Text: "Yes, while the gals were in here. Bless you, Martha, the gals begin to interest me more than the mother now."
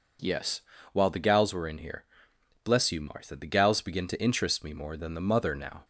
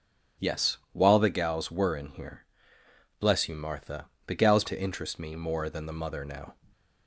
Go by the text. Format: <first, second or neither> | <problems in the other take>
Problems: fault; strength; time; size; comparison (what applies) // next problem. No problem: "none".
first | skips "begin"; at 4.6 s